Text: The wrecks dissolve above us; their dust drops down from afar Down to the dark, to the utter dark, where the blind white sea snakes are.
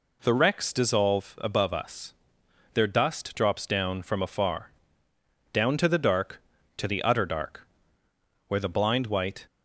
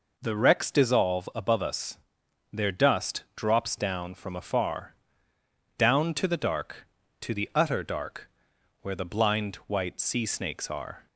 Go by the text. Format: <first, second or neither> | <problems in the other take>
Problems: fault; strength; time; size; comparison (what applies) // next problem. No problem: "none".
second | pauses between "afar" and "Down"; noticeable; at 4.6 s; 0.84 s long; noticeable in the second // stops before "sea snakes are"; at 9.4 s